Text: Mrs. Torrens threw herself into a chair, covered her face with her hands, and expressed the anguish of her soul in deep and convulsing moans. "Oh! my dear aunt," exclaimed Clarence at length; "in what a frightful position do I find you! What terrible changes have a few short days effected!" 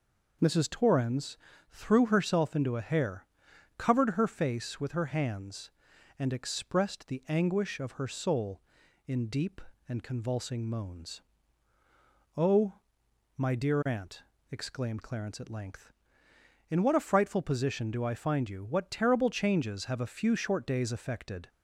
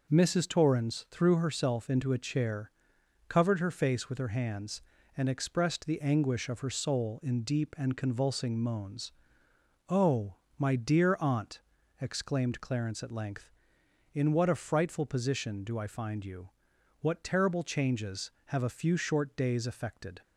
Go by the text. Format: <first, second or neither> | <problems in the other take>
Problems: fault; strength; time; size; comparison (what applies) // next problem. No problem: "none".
second | pauses between "Torrens" and "threw"; slight; at 1.3 s; 0.34 s long // says "hair" for "chair"; at 2.8 s